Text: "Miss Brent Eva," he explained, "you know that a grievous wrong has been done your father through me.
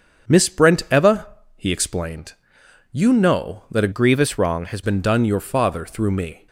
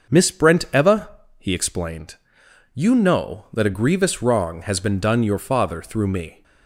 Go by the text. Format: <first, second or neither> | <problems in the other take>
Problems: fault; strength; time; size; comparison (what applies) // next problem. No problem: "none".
second | starts louder than the rest; strong; until 1.6 s; 7 dB; also in the second // changes voice from "grievous" to "has"; from 3.9 to 4.8 s; 0.9 s long